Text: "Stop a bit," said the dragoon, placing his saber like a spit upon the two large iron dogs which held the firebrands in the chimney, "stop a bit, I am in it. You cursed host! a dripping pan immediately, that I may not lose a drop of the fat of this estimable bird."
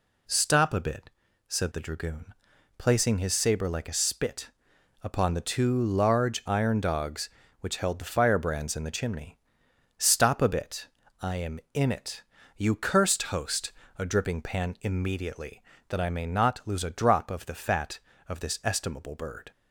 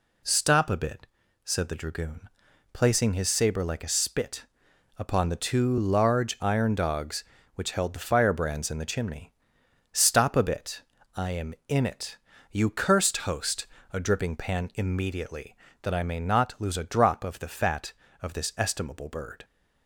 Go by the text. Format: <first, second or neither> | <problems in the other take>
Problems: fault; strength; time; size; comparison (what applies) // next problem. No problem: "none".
neither | pauses between "spit" and "upon"; noticeable; the same in both